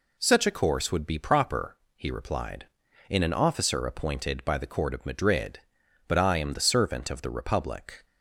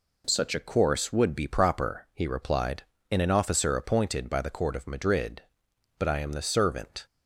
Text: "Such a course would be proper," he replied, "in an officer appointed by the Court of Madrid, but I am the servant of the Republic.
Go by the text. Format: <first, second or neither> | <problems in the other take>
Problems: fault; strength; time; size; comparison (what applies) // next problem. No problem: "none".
first | stops before "of the Republic"; at 7.0 s